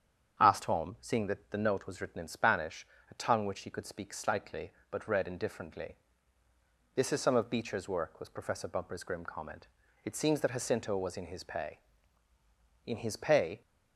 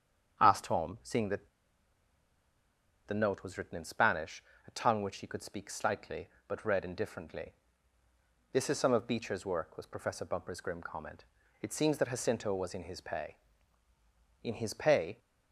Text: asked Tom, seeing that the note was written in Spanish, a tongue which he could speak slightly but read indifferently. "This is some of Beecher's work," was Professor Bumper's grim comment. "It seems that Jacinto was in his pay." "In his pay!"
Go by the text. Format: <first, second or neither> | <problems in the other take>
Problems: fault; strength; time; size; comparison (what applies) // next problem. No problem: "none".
first | starts louder than the rest; strong; until 1.4 s; 8.5 dB; strong in the first // pauses between "that" and "the"; strong; at 1.4 s; 1.5 s long